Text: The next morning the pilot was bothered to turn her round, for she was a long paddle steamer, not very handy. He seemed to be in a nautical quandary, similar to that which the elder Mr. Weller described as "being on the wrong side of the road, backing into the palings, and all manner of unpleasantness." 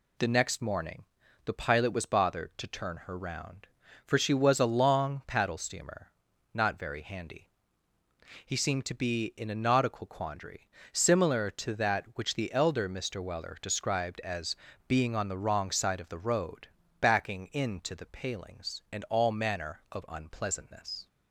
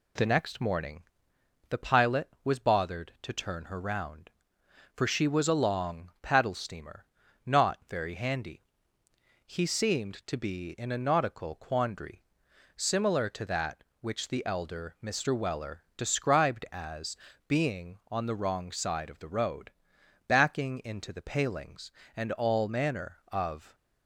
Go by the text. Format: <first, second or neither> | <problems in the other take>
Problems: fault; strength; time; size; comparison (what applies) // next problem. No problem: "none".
first | pauses between "morning" and "the"; noticeable; at 1.0 s; 0.66 s long; also in the first // pauses between "Weller" and "described"; slight; at 15.8 s; 0.16 s long // pauses between "as" and "being"; slight; at 17.1 s; 0.32 s long; slight in the first // stops before "unpleasantness"; at 23.7 s